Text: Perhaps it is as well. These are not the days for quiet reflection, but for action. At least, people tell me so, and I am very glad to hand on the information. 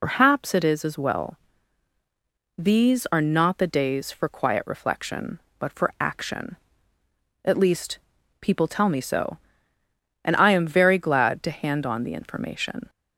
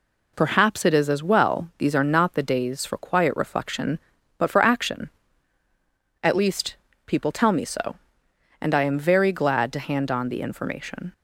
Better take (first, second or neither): second